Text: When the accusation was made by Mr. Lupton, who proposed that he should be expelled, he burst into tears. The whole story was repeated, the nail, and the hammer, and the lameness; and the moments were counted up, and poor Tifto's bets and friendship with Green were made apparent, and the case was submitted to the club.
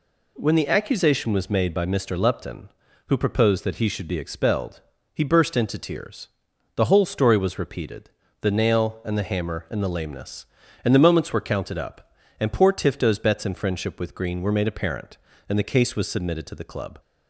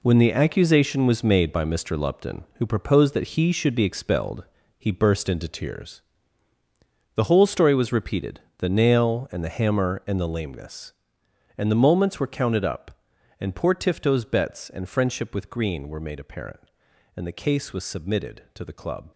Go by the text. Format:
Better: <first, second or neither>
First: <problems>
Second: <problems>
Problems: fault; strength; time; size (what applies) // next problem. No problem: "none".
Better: first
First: none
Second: gets quieter; strong; throughout; 11 dB